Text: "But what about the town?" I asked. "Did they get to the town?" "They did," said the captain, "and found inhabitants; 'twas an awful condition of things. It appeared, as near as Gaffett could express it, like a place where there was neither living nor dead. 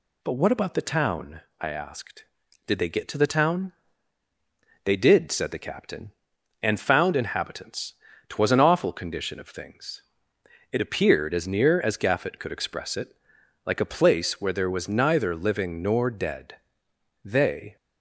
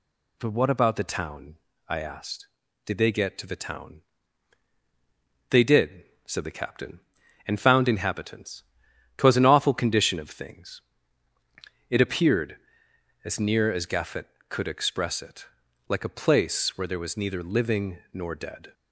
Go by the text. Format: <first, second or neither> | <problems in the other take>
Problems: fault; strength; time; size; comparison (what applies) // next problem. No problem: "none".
second | goes on to say "They"; from 17.2 s on; 0.52 s long